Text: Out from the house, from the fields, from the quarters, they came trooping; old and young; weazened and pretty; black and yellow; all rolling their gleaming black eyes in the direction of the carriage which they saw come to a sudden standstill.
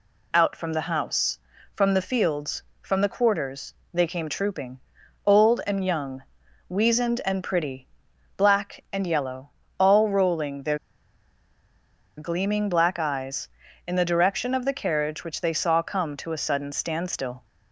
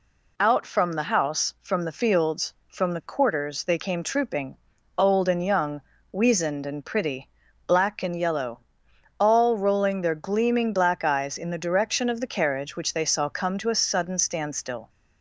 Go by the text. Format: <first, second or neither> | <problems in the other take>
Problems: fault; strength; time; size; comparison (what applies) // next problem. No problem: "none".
second | pauses between "their" and "gleaming"; strong; at 10.7 s; 1.4 s long